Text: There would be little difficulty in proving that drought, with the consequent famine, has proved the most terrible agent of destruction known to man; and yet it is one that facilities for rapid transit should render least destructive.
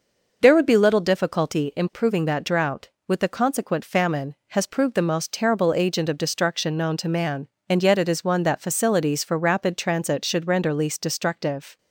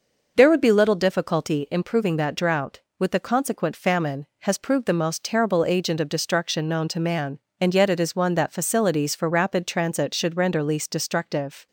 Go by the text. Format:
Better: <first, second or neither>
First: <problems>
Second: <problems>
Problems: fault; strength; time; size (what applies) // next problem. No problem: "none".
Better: neither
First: none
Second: none